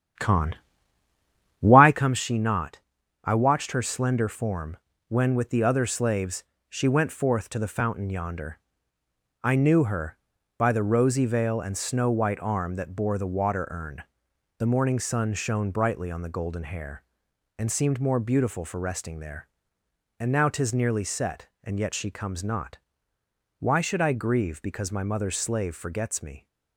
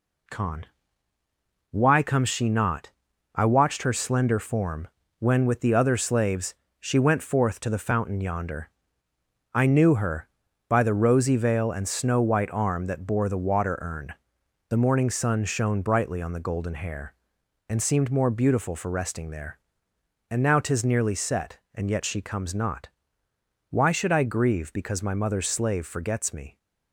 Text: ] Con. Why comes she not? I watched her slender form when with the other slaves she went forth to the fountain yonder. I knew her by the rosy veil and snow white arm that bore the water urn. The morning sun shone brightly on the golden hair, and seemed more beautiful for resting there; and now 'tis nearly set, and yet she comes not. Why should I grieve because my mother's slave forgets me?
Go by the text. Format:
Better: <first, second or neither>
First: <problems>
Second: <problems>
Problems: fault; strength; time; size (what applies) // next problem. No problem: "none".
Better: second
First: starts louder than the rest; strong; until 2.1 s; 9.5 dB // pauses between "form" and "when"; slight; at 4.7 s; 0.32 s long // pauses between "slaves" and "she"; slight; at 6.4 s; 0.24 s long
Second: pauses between "form" and "when"; slight; at 4.8 s; 0.32 s long // pauses between "slaves" and "she"; slight; at 6.5 s; 0.24 s long